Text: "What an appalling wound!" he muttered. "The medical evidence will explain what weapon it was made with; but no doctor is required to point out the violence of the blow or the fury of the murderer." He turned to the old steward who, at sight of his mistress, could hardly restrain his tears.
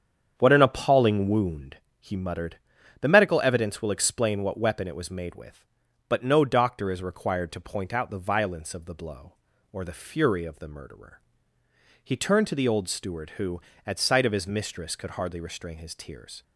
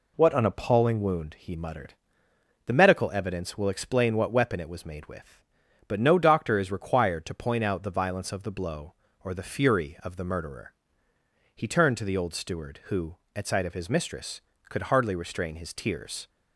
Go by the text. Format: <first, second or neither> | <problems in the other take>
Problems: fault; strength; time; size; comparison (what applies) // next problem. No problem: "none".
second | starts louder than the rest; strong; until 1.8 s; 8 dB